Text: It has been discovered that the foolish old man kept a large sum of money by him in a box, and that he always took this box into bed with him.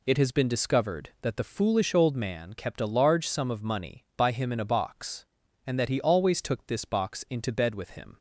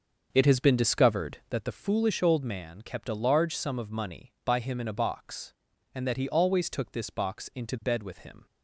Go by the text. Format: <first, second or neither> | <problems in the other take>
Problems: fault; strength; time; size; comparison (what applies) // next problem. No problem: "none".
first | starts louder than the rest; until 1.7 s; 6.5 dB